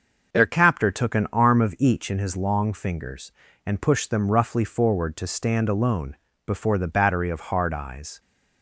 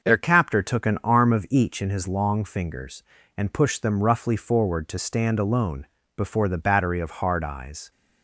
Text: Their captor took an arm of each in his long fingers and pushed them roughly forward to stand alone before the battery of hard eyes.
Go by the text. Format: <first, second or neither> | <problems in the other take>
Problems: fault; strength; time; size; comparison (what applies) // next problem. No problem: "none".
neither | starts louder than the rest; noticeable; the same in both // pauses between "alone" and "before"; slight; the same in both